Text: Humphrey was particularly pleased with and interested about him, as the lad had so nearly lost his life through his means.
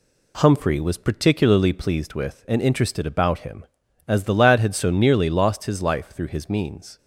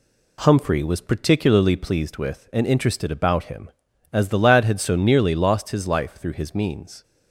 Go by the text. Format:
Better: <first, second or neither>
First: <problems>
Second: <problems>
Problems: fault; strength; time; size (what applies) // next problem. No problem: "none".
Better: neither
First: none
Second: none